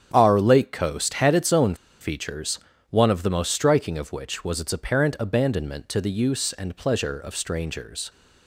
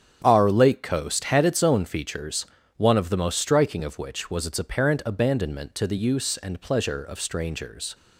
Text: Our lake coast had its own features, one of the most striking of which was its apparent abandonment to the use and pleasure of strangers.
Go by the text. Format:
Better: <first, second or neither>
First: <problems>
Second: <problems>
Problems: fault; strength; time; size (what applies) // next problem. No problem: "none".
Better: second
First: starts louder than the rest; strong; until 1.1 s; 8.5 dB // pauses between "own" and "features"; slight; at 1.7 s; 0.26 s long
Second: starts louder than the rest; strong; until 1.2 s; 8 dB